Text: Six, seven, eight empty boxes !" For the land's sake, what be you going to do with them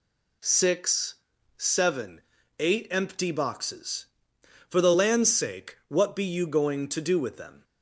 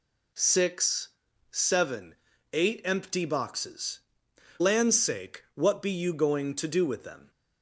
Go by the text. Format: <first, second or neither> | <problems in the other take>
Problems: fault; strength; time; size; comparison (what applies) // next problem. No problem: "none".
first | skips "For the"; at 4.6 s